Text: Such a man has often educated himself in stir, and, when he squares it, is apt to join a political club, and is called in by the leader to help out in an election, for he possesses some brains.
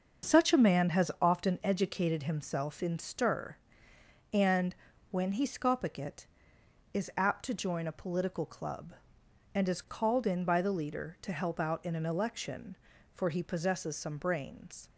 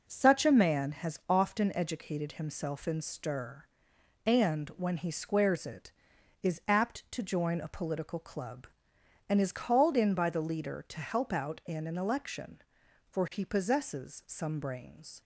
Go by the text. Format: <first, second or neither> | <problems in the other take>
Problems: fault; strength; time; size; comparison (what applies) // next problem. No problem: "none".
second | starts louder than the rest; until 1.3 s; 6.5 dB // says "scopic" for "squares"; at 5.4 s